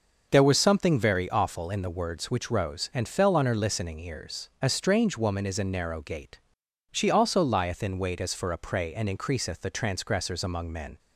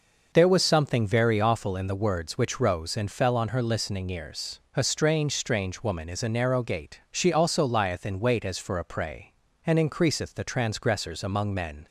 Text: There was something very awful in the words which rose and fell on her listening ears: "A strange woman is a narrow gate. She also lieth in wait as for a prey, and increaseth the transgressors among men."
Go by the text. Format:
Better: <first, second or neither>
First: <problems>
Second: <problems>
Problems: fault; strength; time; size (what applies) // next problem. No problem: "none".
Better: first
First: none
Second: says "strange" twice; at 5.3 s